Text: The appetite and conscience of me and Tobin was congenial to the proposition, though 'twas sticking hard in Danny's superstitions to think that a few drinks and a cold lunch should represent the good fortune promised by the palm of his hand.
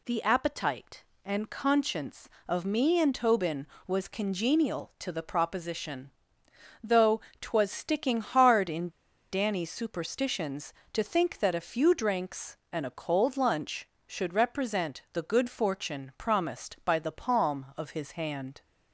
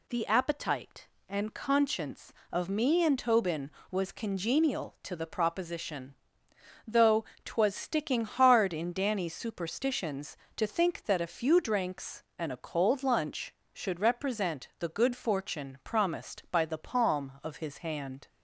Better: second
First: pauses between "though" and "twas"; slight; at 7.2 s; 0.18 s long // pauses between "in" and "Danny's"; at 8.8 s; 0.43 s long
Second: pauses between "though" and "twas"; slight; at 7.2 s; 0.18 s long

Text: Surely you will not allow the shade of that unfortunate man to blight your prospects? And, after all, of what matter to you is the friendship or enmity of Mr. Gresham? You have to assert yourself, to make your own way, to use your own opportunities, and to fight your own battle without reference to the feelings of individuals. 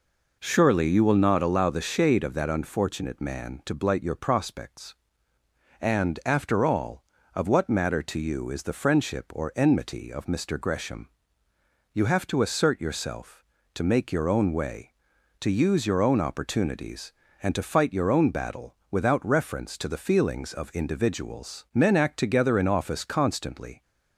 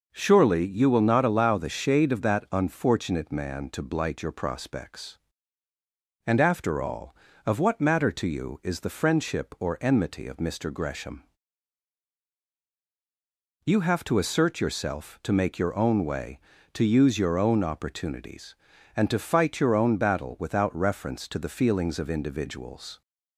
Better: second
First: pauses between "battle" and "without"; slight; at 18.7 s; 0.16 s long // goes on to say "Men act together in office constantly"; strong; from 21.7 s on; 2.0 s long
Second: none

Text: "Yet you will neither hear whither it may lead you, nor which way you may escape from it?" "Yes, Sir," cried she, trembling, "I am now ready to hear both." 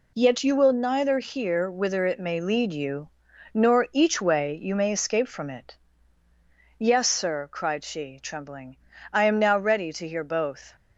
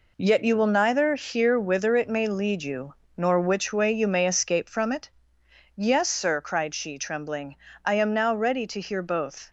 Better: second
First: says "each" for "which"; at 3.9 s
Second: none

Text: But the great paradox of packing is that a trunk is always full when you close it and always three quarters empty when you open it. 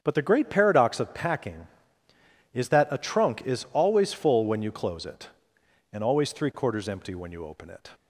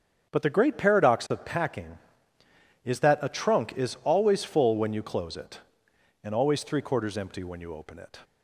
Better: neither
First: starts louder than the rest; strong; until 1.0 s; 7.5 dB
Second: starts louder than the rest; strong; until 1.3 s; 7.5 dB

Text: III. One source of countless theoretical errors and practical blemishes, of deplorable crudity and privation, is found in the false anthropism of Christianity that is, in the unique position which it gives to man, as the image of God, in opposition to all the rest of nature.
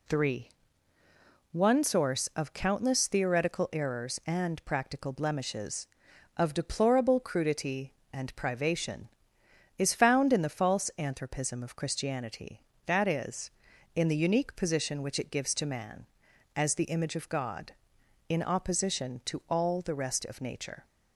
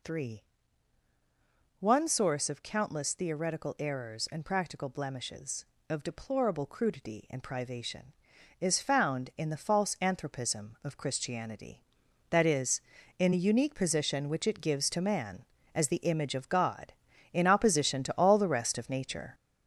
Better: first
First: none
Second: gets louder; noticeable; throughout; 6 dB

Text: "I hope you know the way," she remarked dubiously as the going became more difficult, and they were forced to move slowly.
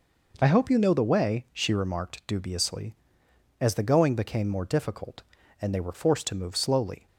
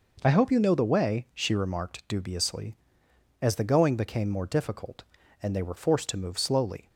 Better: neither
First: none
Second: none

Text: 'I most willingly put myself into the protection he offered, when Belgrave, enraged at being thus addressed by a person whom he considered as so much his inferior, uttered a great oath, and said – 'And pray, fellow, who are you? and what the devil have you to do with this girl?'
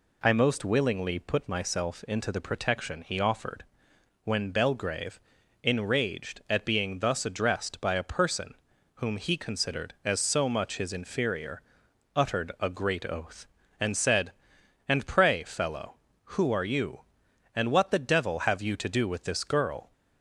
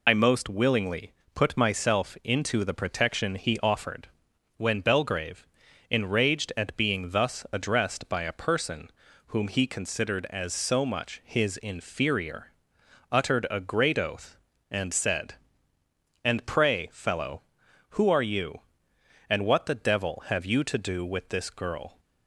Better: first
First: pauses between "person" and "whom"; at 8.5 s; 0.42 s long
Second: loses the start of "I"; at 0.0 s; 65 ms // pauses between "willingly" and "put"; slight; at 1.1 s; 0.22 s long // pauses between "person" and "whom"; at 8.8 s; 0.38 s long

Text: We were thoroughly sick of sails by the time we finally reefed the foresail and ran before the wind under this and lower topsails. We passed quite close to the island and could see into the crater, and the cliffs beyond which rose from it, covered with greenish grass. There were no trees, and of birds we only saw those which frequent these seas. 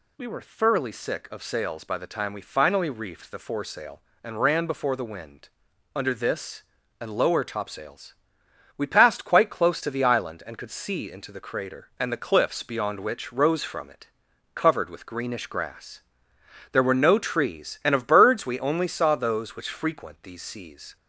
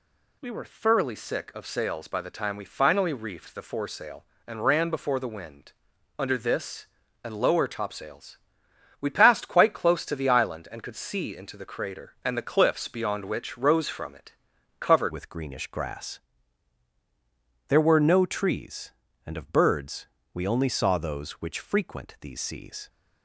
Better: first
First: pauses between "wind" and "under"; noticeable; at 5.4 s; 0.48 s long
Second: pauses between "wind" and "under"; noticeable; at 5.7 s; 0.48 s long // changes voice at "with"; from 15.1 s on; 7.7 s long // pauses between "birds" and "we"; slight; at 20.0 s; 0.26 s long

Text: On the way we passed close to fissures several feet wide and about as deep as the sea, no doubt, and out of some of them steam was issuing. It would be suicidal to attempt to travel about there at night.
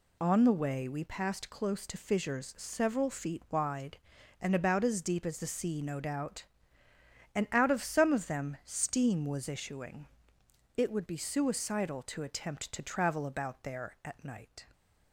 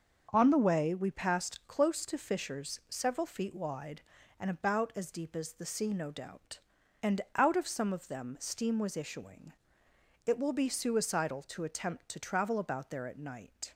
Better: first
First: none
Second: starts louder than the rest; until 1.3 s; 6.5 dB // says "will" for "would"; at 10.3 s

